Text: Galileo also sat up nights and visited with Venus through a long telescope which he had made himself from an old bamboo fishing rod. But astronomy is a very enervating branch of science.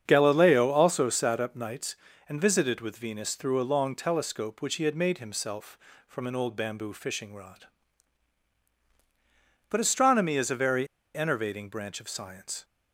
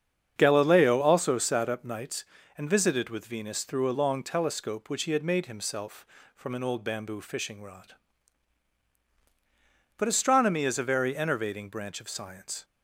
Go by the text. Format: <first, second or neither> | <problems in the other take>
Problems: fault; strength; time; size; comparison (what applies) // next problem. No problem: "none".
second | starts louder than the rest; strong; until 1.0 s; 7.5 dB; strong in the second // pauses between "very" and "enervating"; slight; at 10.8 s; 0.29 s long